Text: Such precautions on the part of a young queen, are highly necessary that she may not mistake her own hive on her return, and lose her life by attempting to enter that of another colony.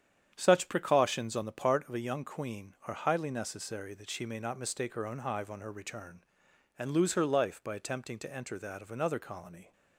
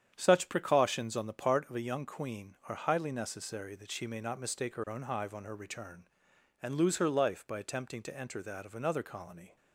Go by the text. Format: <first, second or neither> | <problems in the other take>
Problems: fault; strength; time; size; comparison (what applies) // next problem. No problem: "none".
neither | starts louder than the rest; strong; the same in both